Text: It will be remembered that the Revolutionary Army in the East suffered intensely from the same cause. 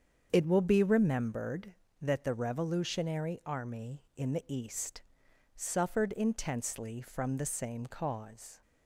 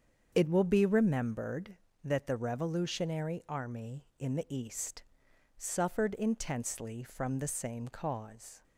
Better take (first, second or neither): neither